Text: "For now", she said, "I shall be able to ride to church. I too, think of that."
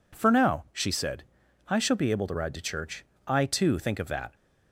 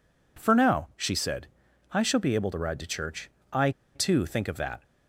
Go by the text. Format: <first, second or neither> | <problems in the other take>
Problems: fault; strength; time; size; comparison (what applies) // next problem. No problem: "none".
first | pauses between "I" and "too"; slight; at 3.7 s; 0.23 s long